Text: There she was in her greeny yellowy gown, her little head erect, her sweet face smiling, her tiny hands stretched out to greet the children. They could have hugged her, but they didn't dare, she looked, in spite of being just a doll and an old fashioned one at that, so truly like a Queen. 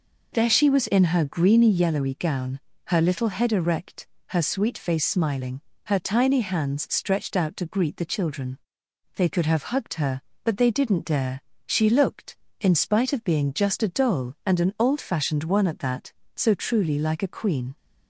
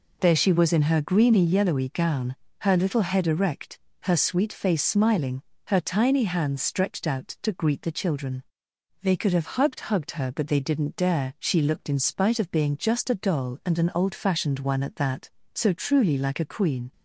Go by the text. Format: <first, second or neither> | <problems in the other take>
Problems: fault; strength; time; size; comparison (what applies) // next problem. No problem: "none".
first | says "hugged" twice; at 9.7 s